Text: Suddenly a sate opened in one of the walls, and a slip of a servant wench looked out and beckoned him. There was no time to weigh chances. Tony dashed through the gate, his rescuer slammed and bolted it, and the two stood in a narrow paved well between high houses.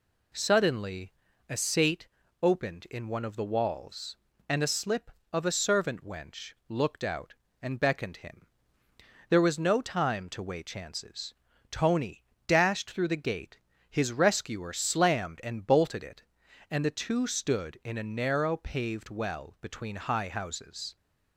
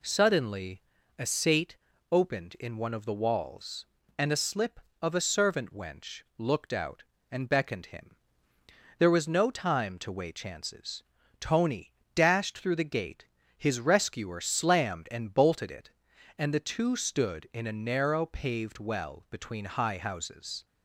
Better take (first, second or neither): neither